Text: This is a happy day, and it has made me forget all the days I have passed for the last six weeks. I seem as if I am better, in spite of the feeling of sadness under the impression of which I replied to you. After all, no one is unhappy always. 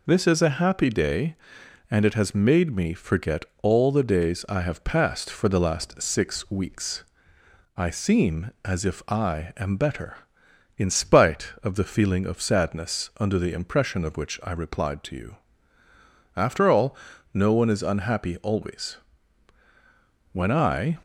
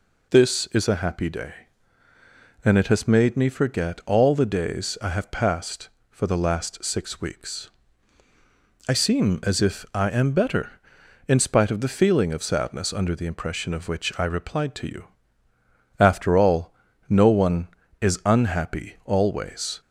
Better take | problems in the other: second | pauses between "forget" and "all"; slight; at 3.4 s; 0.16 s long // goes on to say "When I"; noticeable; from 20.3 s on; 0.64 s long

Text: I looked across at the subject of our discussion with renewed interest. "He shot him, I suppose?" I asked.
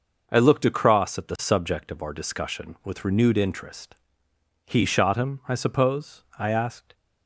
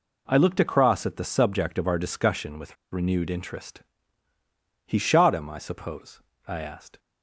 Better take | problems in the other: first | pauses between "with" and "renewed"; slight; at 2.7 s; 0.16 s long

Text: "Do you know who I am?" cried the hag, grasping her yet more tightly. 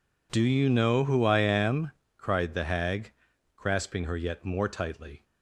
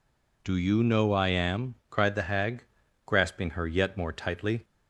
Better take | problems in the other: first | skips "who"; at 1.1 s

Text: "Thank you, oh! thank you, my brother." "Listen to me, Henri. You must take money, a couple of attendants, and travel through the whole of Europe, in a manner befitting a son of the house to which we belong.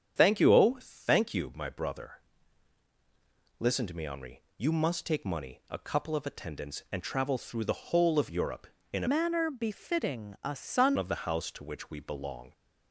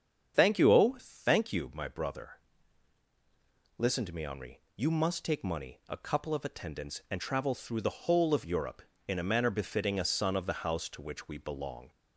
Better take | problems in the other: second | starts louder than the rest; strong; until 1.1 s; 8 dB; strong in the second // changes voice from "manner" to "son"; from 9.0 to 10.9 s; 1.9 s long

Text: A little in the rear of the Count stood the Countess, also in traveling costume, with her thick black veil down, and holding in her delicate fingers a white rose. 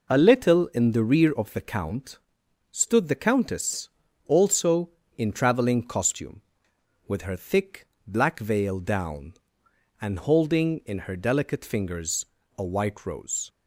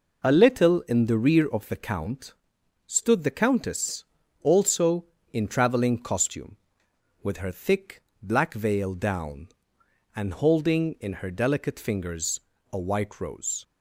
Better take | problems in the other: neither | pauses between "Count" and "stood"; noticeable; the same in both // pauses between "thick" and "black"; slight; the same in both // pauses between "fingers" and "a"; slight; the same in both

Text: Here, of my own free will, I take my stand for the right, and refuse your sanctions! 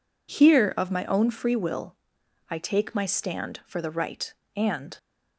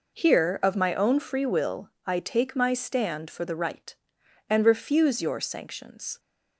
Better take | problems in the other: second | stops before "refuse your sanctions"; at 4.9 s

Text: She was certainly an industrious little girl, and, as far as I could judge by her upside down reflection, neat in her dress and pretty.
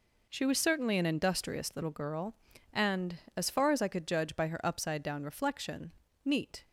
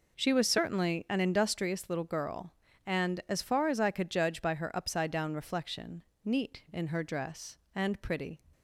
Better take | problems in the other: second | stops before "in her dress and pretty"; at 6.6 s

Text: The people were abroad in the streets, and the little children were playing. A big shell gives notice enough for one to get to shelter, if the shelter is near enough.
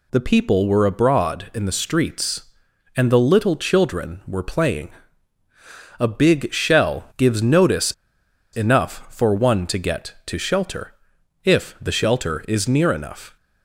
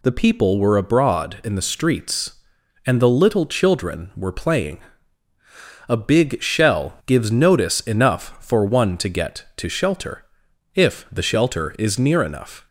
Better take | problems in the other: second | pauses between "notice" and "enough"; noticeable; at 7.9 s; 0.61 s long

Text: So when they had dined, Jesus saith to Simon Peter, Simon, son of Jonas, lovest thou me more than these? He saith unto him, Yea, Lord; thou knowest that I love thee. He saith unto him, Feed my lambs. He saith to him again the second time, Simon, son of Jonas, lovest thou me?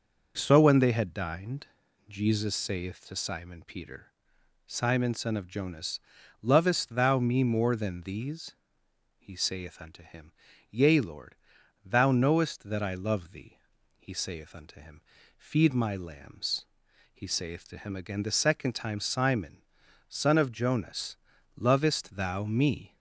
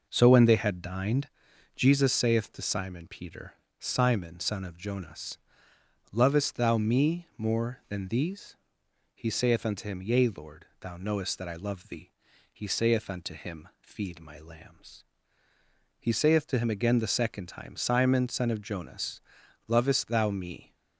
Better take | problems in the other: neither | none

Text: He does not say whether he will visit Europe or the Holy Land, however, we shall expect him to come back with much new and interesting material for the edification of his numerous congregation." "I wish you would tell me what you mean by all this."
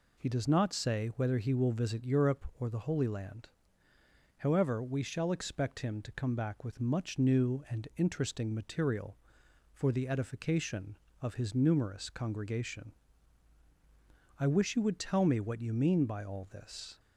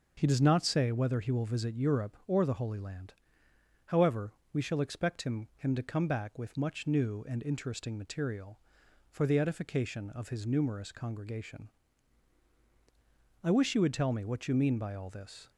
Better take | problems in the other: first | starts louder than the rest; until 1.1 s; 6 dB // says "him" twice; at 5.5 s

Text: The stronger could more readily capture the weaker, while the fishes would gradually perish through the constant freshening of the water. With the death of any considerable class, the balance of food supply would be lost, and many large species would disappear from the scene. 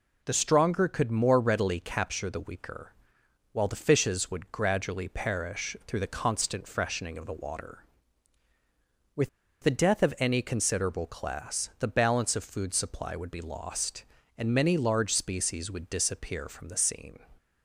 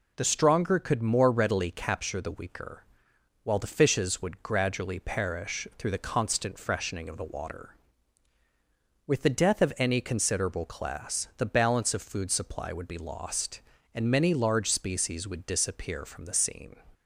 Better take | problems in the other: second | pauses between "With" and "the"; slight; at 9.2 s; 0.35 s long

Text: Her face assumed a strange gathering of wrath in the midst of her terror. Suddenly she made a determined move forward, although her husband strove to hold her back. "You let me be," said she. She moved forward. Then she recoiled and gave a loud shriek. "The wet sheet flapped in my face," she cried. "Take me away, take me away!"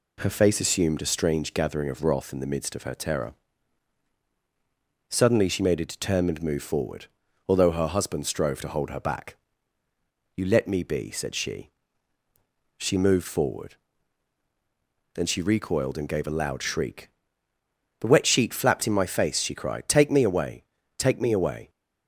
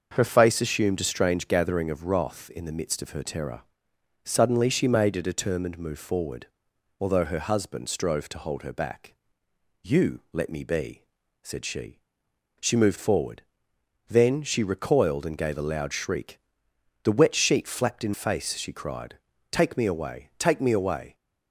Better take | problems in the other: first | starts louder than the rest; until 1.1 s; 6.5 dB // skips "my"; at 18.1 s

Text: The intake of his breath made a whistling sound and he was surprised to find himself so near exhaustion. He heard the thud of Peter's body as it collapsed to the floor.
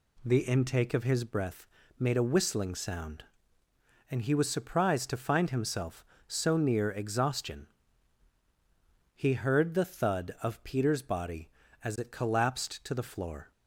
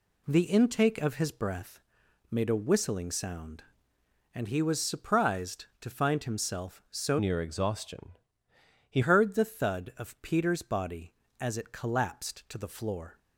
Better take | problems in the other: first | pauses between "breath" and "made"; noticeable; at 1.8 s; 0.50 s long; slight in the first // changes voice from "near" to "He"; from 7.1 to 9.0 s; 1.9 s long

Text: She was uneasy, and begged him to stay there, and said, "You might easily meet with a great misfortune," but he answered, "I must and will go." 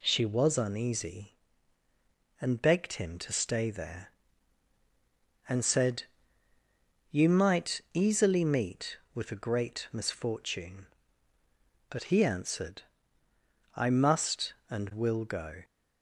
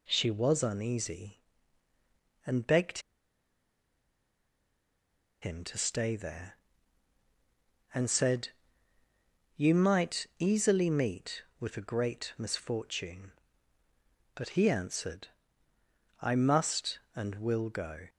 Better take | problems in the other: first | pauses between "begged" and "him"; strong; at 2.9 s; 2.4 s long

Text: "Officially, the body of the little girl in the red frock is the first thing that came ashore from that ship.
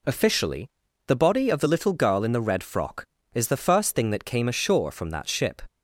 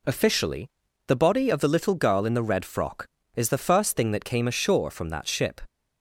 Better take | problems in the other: neither | none

